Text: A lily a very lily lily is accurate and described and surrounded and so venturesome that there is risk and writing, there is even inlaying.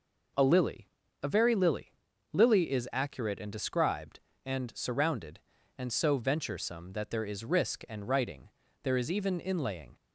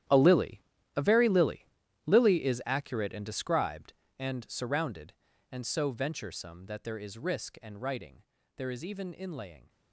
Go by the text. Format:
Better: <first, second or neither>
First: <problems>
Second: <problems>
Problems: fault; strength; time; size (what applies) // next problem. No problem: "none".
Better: first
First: pauses between "lily" and "a"; slight; at 0.8 s; 0.34 s long // pauses between "lily" and "lily"; at 1.9 s; 0.40 s long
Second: gets quieter; strong; throughout; 15.5 dB // pauses between "lily" and "a"; slight; at 0.6 s; 0.34 s long // pauses between "lily" and "lily"; at 1.6 s; 0.40 s long